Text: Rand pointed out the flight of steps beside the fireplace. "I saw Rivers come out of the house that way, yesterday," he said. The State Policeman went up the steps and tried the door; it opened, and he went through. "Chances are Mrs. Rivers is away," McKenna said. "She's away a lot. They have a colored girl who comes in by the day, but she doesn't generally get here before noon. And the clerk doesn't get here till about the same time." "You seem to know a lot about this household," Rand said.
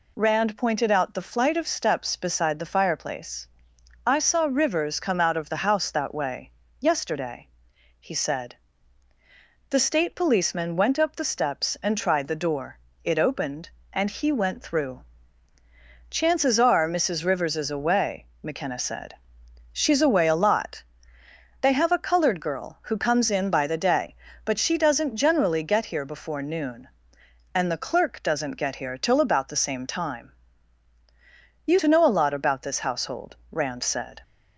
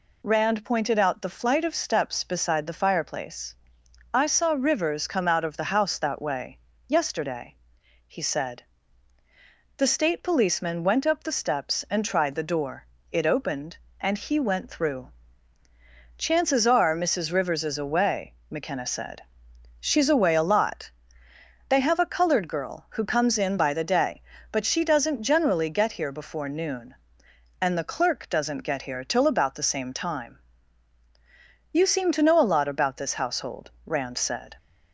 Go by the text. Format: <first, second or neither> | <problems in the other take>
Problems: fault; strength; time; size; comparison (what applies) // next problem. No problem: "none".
second | skips "seem"; at 31.7 s